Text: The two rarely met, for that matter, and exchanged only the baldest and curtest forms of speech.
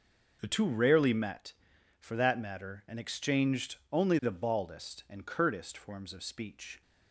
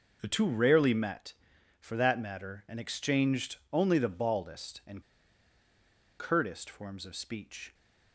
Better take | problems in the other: first | pauses between "exchanged" and "only"; slight; at 3.5 s; 0.16 s long; slight in the first // pauses between "and" and "curtest"; at 5.0 s; 1.1 s long

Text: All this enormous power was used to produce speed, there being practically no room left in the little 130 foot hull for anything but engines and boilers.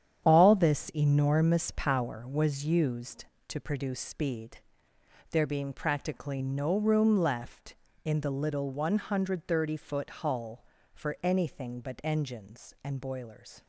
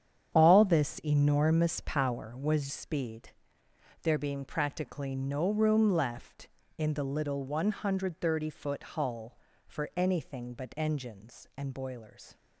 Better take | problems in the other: first | starts louder than the rest; strong; until 1.4 s; 9 dB; strong in the first // skips "used to produce"; at 2.7 s

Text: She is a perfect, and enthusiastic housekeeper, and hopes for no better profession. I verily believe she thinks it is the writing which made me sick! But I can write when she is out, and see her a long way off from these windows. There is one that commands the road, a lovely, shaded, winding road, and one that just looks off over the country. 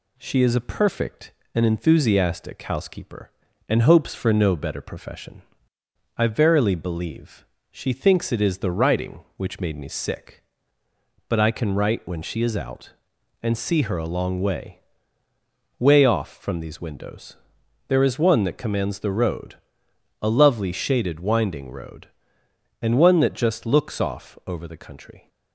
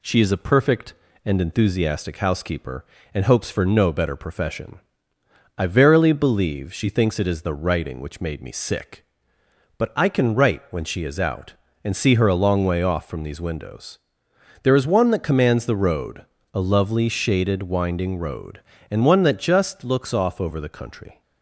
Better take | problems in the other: second | pauses between "believe" and "she"; slight; at 7.4 s; 0.24 s long // says "way" twice; at 15.7 s

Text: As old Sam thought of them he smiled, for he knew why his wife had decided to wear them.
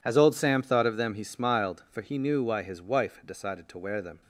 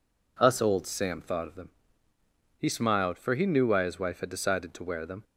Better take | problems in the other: first | says "Us" for "As"; at 0.3 s // pauses between "them" and "he"; noticeable; at 1.6 s; 0.90 s long

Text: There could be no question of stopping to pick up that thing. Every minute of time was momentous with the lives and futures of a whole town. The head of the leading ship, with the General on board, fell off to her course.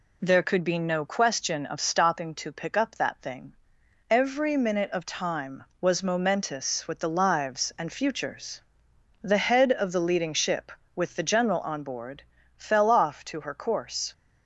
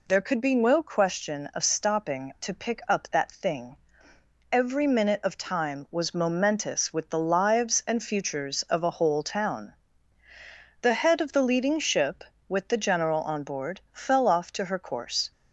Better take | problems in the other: second | skips "of a whole town"; at 8.9 s

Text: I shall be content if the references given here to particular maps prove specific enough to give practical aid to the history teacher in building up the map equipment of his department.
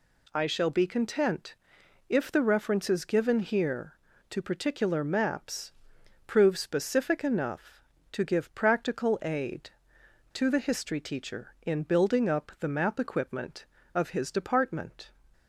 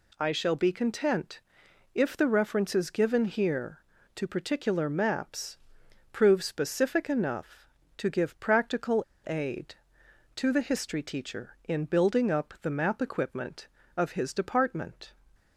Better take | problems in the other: first | pauses between "content" and "if"; noticeable; at 1.4 s; 0.54 s long; noticeable in the first // pauses between "maps" and "prove"; noticeable; at 5.5 s; 0.56 s long; noticeable in the first // pauses between "practical" and "aid"; slight; at 9.0 s; 0.23 s long

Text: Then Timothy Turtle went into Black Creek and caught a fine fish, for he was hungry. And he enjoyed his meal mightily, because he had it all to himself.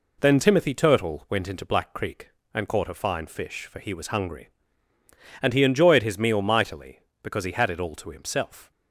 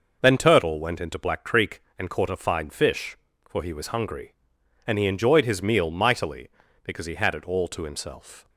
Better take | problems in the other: first | skips "Timothy"; at 0.3 s

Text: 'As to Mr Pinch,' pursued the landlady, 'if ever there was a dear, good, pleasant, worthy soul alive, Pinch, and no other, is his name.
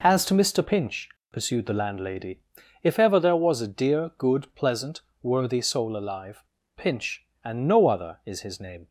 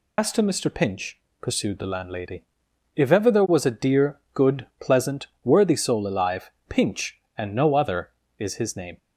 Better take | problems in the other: first | loses the start of "As"; at 0.1 s; 105 ms

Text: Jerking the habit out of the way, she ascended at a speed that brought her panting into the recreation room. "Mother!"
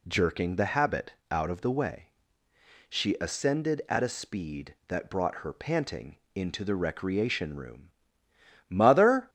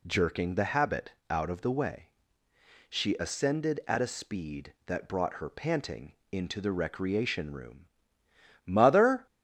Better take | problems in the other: neither | pauses between "habit" and "out"; slight; the same in both // pauses between "panting" and "into"; slight; the same in both

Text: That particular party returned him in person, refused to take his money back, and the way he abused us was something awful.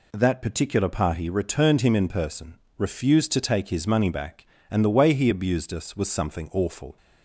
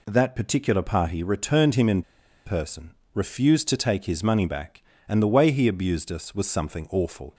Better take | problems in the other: first | pauses between "in" and "person"; at 2.0 s; 0.44 s long

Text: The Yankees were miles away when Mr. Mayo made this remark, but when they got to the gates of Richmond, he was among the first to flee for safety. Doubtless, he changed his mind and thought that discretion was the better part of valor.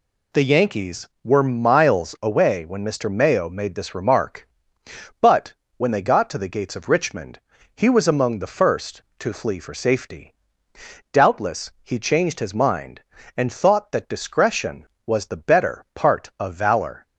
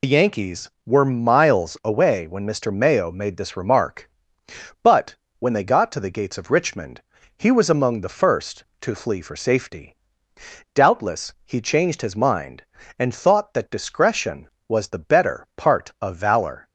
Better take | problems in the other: first | loses the start of "The"; at 0.0 s; 85 ms // pauses between "but" and "when"; slight; at 5.1 s; 0.24 s long; slight in the first

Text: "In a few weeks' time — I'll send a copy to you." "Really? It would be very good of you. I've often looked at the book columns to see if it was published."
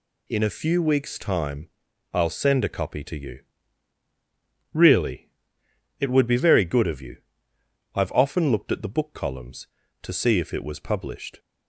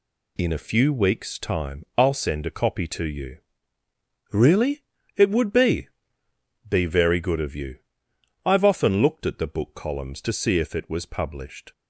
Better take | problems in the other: first | says "be" twice; at 6.6 s

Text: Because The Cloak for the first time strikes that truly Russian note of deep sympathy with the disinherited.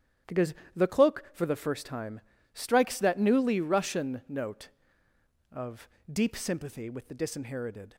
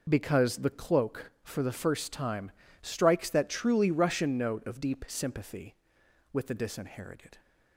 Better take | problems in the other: second | starts louder than the rest; strong; until 1.5 s; 10.5 dB // pauses between "Because" and "The"; slight; at 0.5 s; 0.22 s long // pauses between "time" and "strikes"; slight; at 2.1 s; 0.34 s long; slight in the second // says "newly" for "truly"; at 3.1 s // pauses between "of" and "deep"; slight; at 5.8 s; 0.23 s long

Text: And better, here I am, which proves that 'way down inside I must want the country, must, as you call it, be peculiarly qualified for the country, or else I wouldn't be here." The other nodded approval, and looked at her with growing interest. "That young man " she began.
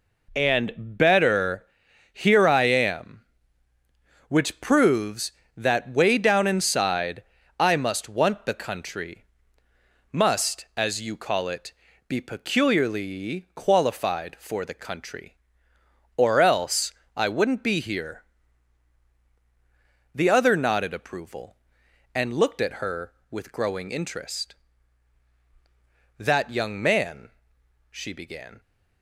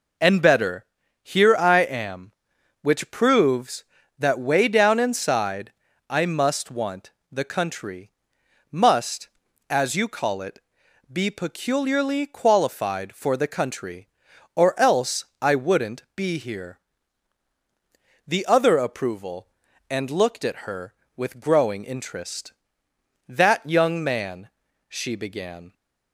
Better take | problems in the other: first | pauses between "inside" and "I"; slight; at 5.7 s; 0.36 s long; slight in the first // pauses between "want" and "the"; slight; at 7.1 s; 0.20 s long // pauses between "else" and "I"; slight; at 15.2 s; 0.18 s long; slight in the first // skips "nodded"; at 18.7 s

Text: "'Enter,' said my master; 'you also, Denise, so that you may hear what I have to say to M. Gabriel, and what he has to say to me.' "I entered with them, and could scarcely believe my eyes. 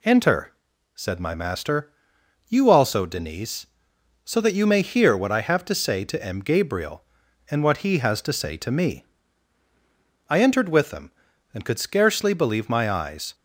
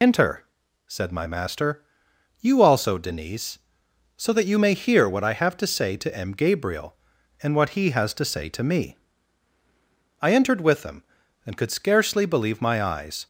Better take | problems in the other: first | loses the start of "Enter"; at 0.0 s; 65 ms

